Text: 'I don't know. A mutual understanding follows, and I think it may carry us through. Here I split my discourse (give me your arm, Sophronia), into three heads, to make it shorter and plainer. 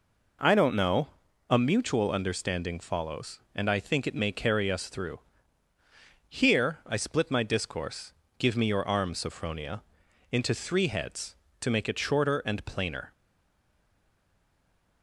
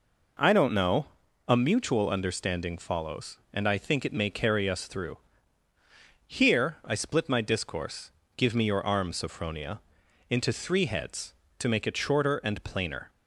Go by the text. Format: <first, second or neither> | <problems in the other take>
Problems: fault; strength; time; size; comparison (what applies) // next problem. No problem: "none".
second | stays silent after the last word; noticeable; from 13.1 s on; 1.9 s long